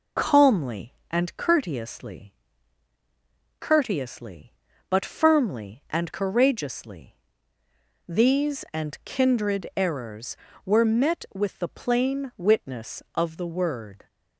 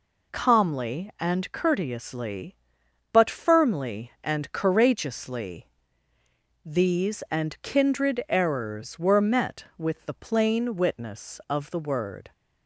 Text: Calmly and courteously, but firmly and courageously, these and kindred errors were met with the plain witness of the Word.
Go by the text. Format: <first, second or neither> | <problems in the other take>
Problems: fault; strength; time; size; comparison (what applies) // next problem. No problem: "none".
second | says "courteously" twice; at 3.6 s